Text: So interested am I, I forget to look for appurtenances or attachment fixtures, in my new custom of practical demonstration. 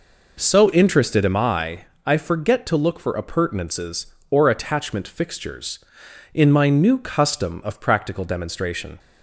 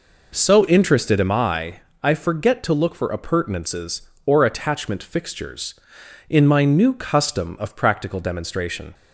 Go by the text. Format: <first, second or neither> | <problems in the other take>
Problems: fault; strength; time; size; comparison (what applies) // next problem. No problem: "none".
neither | none